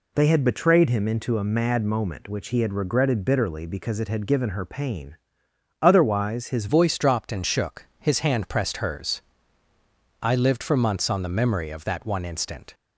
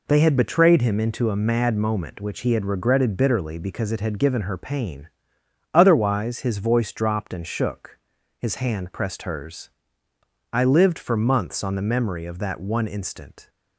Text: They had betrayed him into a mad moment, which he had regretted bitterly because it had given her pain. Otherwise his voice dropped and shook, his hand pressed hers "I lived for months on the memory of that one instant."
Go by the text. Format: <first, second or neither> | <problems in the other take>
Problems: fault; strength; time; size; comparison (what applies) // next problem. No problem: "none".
second | changes voice at "voice"; from 6.6 s on; 6.1 s long // pauses between "hers" and "I"; at 9.2 s; 1.0 s long; noticeable in the second